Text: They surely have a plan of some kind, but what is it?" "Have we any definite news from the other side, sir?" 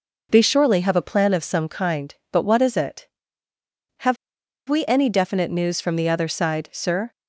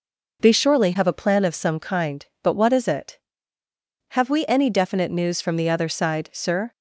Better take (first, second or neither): second